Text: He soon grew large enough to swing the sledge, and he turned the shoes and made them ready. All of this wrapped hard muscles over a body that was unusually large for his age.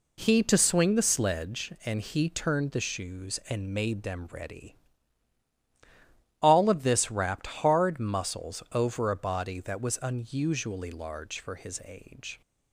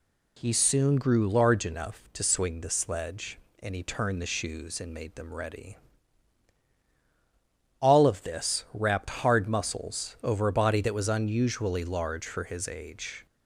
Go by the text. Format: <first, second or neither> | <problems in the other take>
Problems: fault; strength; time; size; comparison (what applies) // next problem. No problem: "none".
second | skips "soon grew large enough"; at 0.4 s